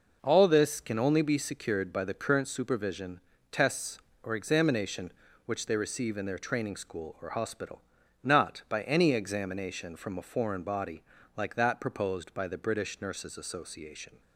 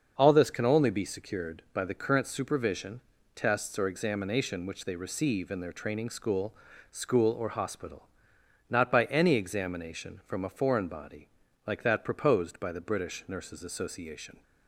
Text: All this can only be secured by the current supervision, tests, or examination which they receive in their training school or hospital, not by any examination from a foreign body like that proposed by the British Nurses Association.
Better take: first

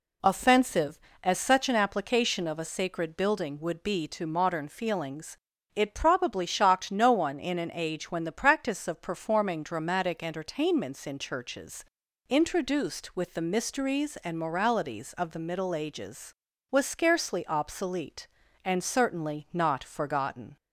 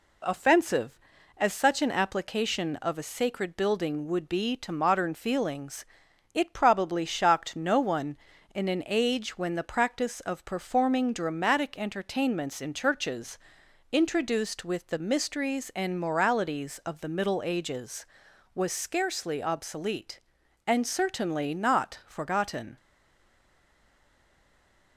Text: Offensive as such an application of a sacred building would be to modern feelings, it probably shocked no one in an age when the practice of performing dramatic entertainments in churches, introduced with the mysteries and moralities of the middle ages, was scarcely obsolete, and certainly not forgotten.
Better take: first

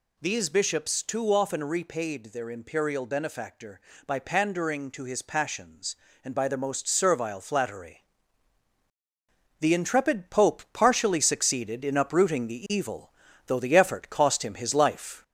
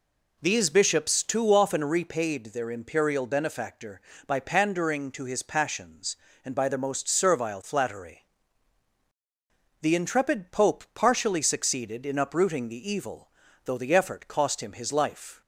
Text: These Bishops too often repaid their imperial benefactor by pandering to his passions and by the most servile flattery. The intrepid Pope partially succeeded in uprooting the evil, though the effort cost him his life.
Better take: second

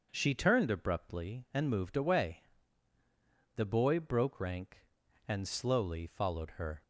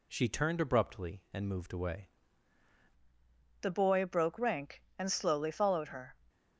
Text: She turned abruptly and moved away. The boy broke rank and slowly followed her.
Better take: first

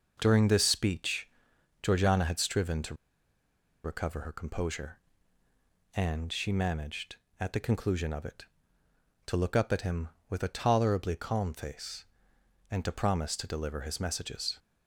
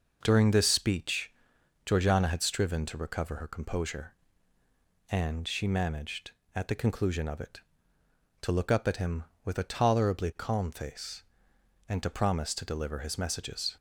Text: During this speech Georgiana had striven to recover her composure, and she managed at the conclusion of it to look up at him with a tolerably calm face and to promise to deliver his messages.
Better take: second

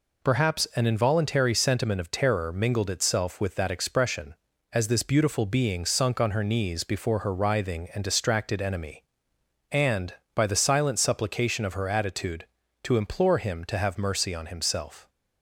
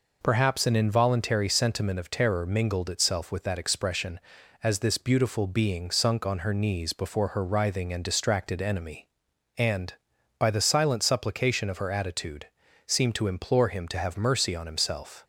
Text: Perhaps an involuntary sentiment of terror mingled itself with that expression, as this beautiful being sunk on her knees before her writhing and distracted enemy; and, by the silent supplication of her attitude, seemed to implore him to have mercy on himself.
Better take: second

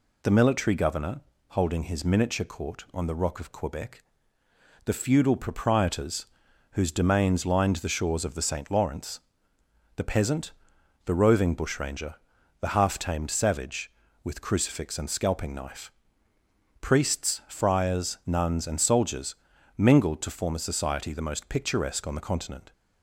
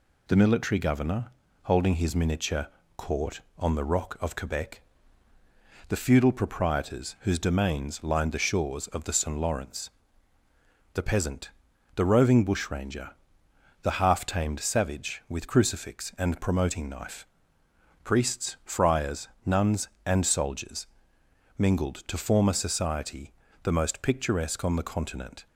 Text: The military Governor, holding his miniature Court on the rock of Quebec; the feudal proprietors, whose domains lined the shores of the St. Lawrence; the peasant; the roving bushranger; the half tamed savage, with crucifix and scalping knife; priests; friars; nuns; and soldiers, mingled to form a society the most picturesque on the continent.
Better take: first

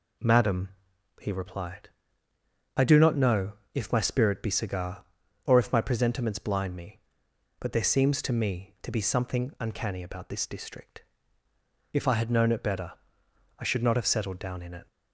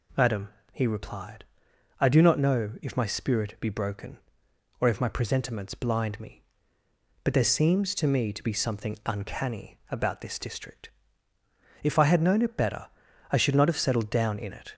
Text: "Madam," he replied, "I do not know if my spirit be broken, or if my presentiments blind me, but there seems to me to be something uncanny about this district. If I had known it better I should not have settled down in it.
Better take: second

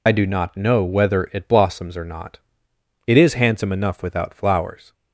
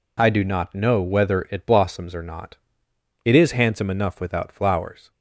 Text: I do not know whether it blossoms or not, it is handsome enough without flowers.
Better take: second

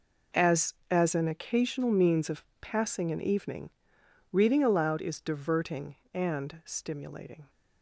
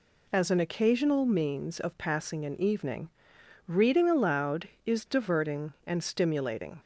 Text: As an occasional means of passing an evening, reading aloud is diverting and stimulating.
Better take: second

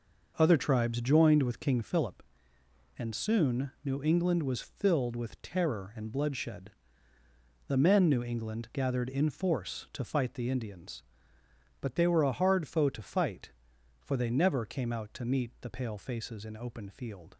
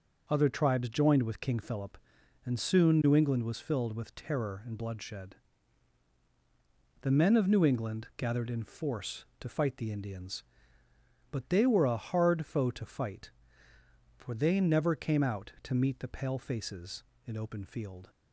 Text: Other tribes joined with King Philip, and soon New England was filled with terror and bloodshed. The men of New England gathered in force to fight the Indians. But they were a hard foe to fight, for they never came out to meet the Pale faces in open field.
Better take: second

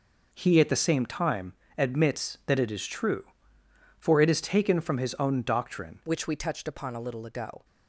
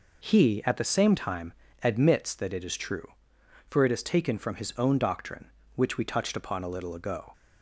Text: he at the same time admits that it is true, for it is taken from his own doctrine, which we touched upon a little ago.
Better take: second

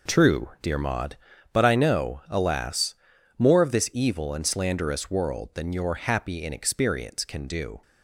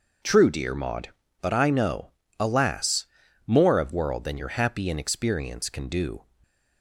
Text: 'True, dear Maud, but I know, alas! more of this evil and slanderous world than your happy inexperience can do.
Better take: first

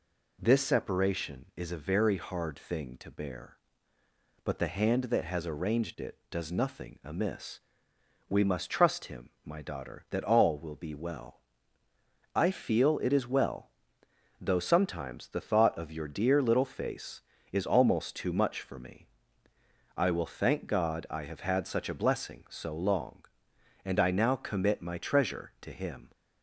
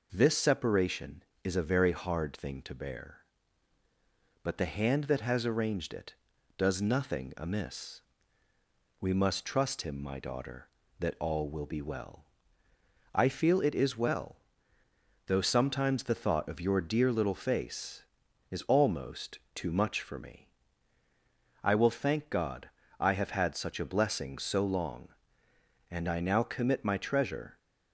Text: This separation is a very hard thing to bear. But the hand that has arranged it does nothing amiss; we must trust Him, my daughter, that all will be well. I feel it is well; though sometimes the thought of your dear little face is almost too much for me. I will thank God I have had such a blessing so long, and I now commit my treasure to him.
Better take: first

